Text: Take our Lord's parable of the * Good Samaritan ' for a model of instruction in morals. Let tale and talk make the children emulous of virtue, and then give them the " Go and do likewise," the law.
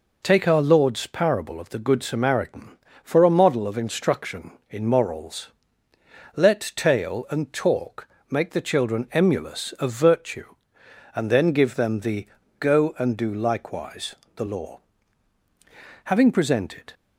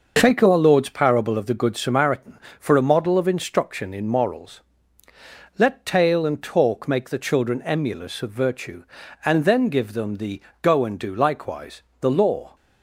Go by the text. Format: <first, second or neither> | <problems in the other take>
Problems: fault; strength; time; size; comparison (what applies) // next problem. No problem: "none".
second | pauses between "talk" and "make"; slight; at 8.0 s; 0.22 s long // goes on to say "Having presented"; noticeable; from 16.0 s on; 0.88 s long